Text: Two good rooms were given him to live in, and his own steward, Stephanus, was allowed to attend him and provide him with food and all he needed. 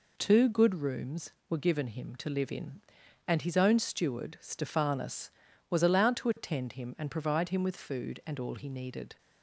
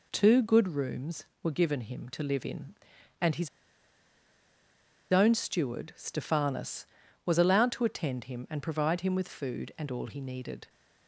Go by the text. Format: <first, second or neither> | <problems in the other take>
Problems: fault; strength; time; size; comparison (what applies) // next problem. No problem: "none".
first | pauses between "his" and "own"; strong; at 3.4 s; 1.6 s long